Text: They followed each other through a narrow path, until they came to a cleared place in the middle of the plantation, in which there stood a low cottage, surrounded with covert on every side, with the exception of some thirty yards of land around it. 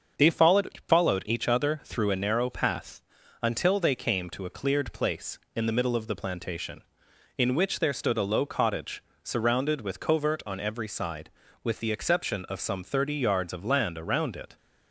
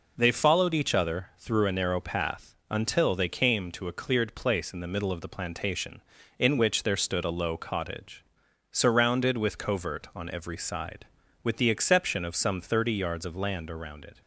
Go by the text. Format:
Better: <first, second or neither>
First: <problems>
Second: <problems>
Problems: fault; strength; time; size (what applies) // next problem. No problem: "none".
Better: second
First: starts louder than the rest; until 1.2 s; 6.5 dB // says "followed" twice; at 0.8 s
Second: none